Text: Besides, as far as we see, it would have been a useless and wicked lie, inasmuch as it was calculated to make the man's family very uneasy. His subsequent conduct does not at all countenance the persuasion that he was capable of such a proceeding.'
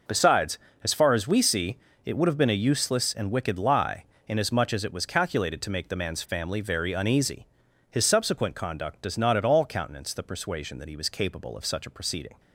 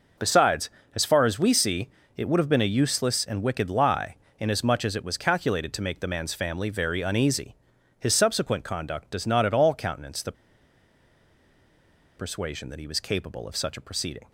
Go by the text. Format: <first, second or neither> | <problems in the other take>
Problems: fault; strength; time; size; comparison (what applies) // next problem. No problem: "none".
first | pauses between "the" and "persuasion"; strong; at 10.3 s; 1.8 s long